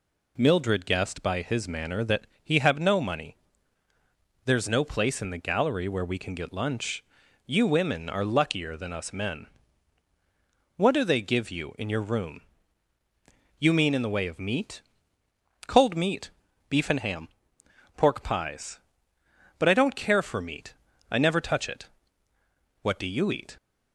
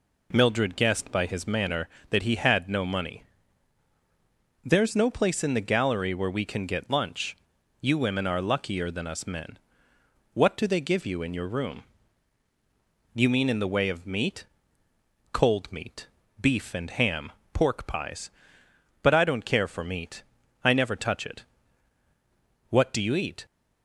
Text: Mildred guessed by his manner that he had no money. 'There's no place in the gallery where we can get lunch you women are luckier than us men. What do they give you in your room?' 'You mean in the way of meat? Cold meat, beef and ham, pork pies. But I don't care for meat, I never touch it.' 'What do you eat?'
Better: second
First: pauses between "that" and "he"; slight; at 2.2 s; 0.18 s long // says "have" for "had"; at 2.5 s // pauses between "lunch" and "you"; noticeable; at 7.0 s; 0.46 s long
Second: pauses between "lunch" and "you"; noticeable; at 7.3 s; 0.48 s long

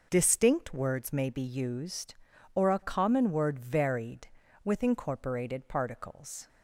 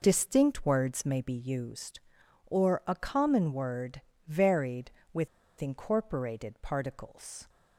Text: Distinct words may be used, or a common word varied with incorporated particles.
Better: first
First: none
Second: pauses between "word" and "varied"; slight; at 4.0 s; 0.26 s long // pauses between "with" and "incorporated"; slight; at 5.2 s; 0.32 s long

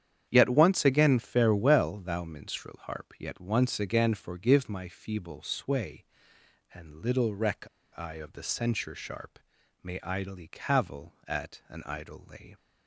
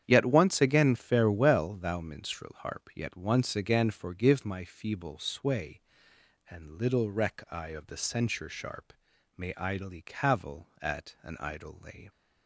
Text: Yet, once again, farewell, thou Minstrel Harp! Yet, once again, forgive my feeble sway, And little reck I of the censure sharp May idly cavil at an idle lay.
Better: second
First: starts louder than the rest; strong; until 1.3 s; 9 dB // pauses between "reck" and "I"; slight; at 7.6 s; 0.30 s long // pauses between "sharp" and "May"; at 9.3 s; 0.42 s long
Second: starts louder than the rest; strong; until 1.0 s; 9 dB // pauses between "sharp" and "May"; at 8.9 s; 0.42 s long

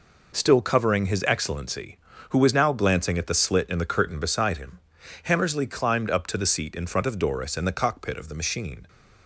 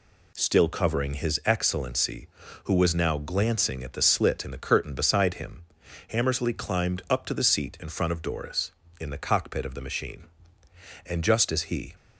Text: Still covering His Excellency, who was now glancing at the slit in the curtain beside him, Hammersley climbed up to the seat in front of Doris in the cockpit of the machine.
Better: first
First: none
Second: goes on to say "And just as he"; noticeable; from 11.0 s on; 0.86 s long

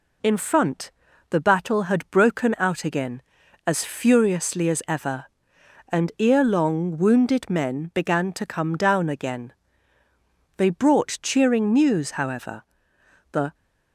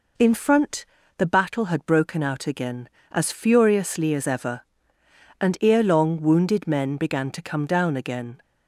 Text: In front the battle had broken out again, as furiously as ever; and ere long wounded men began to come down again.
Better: second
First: pauses between "front" and "the"; at 0.8 s; 0.40 s long // goes on to say "They brought cheering news however The"; strong; from 10.5 s on; 2.9 s long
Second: pauses between "front" and "the"; slight; at 0.8 s; 0.32 s long

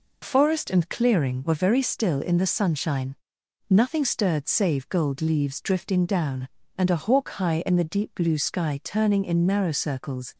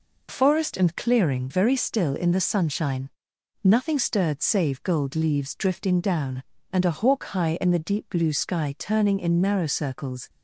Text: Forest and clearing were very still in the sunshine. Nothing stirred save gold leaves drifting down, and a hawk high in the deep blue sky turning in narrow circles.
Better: first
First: none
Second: skips "were"; at 1.4 s

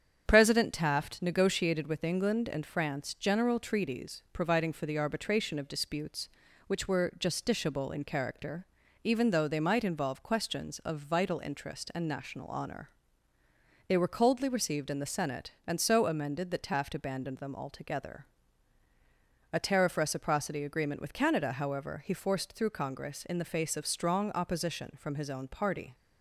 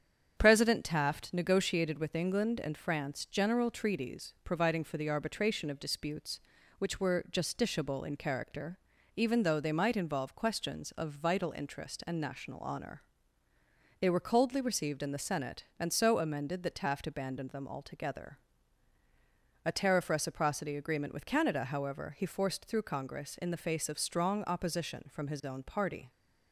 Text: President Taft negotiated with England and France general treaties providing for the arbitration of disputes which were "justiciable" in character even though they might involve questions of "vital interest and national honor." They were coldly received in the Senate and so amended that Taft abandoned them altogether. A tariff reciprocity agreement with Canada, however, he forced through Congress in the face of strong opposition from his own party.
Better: neither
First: starts louder than the rest; strong; until 1.2 s; 8 dB // pauses between "character" and "even"; at 8.6 s; 0.38 s long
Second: starts louder than the rest; strong; until 1.3 s; 8 dB // pauses between "character" and "even"; at 8.7 s; 0.38 s long

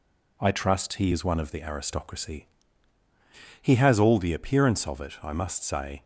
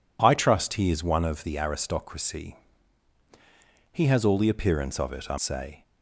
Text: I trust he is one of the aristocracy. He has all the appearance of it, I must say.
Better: first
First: none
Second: skips "must"; at 5.3 s

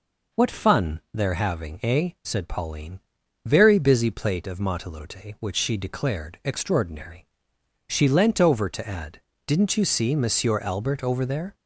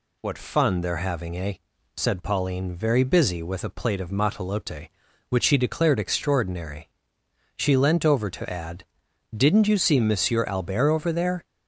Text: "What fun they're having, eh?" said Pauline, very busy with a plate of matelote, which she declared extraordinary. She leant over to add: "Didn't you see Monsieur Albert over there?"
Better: second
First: skips "with a"; at 4.1 s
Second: none

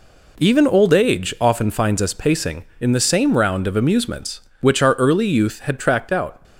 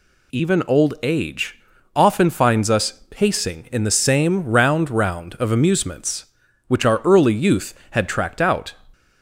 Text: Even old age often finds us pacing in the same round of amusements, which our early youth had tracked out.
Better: first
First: none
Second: pauses between "age" and "often"; slight; at 1.5 s; 0.34 s long // says "round" twice; at 4.8 s

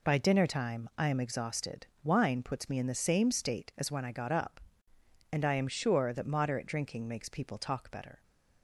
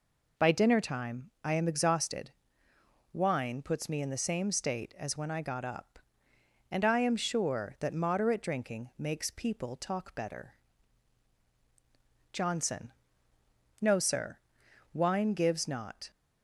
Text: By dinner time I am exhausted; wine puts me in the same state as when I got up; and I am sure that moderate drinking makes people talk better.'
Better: first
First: none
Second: goes on to say "JOHNSON No Sir wine gives not"; strong; from 12.3 s on; 3.7 s long

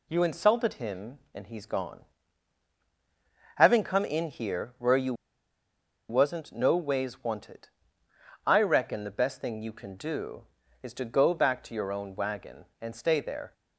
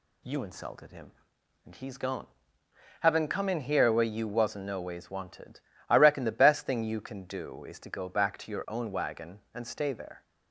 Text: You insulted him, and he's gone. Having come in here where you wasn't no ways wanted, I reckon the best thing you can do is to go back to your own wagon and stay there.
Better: second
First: pauses between "you" and "wasn't"; noticeable; at 5.1 s; 0.95 s long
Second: none

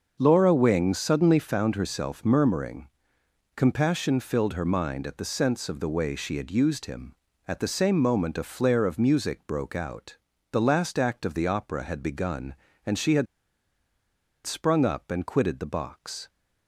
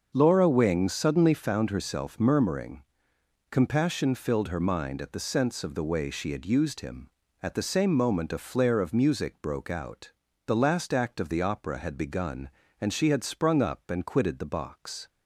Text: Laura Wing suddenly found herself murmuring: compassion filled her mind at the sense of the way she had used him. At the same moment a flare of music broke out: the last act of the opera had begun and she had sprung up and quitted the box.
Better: second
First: starts louder than the rest; until 1.2 s; 6.5 dB // pauses between "had" and "sprung"; at 13.2 s; 1.1 s long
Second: starts louder than the rest; until 1.1 s; 6.5 dB

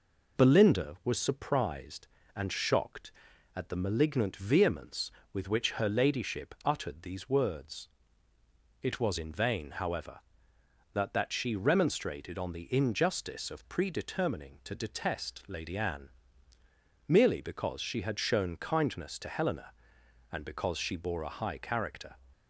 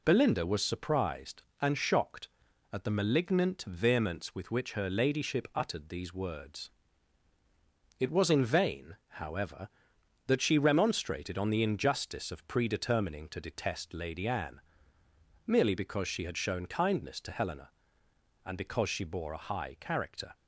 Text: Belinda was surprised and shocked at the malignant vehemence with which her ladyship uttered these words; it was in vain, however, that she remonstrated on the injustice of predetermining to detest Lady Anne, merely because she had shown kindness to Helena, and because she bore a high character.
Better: second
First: says "that" twice; at 11.1 s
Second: none

